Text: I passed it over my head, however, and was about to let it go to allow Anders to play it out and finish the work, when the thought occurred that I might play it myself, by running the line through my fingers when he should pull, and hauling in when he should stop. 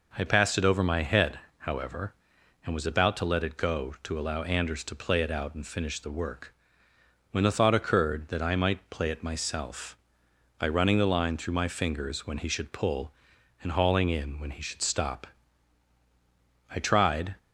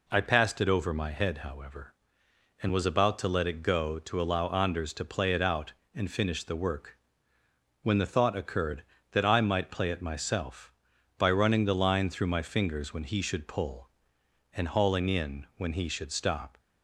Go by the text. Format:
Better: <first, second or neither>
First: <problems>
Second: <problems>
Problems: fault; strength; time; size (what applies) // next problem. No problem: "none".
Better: second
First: goes on to say "I tried"; noticeable; from 16.7 s on; 0.62 s long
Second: none